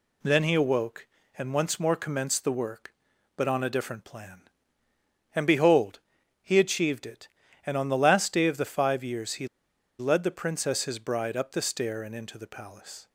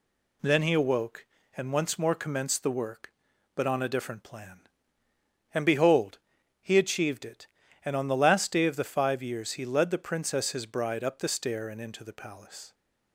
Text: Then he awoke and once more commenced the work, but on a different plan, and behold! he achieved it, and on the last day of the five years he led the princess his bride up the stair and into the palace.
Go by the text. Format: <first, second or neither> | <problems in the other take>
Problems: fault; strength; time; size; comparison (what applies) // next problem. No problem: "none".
second | pauses between "he" and "led"; noticeable; at 9.4 s; 0.52 s long